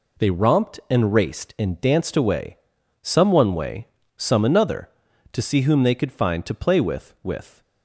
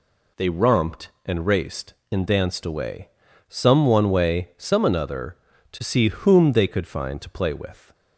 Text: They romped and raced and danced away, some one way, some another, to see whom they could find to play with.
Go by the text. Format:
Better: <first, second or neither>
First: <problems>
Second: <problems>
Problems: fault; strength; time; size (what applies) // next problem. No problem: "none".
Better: second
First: says "with" twice; at 7.2 s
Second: none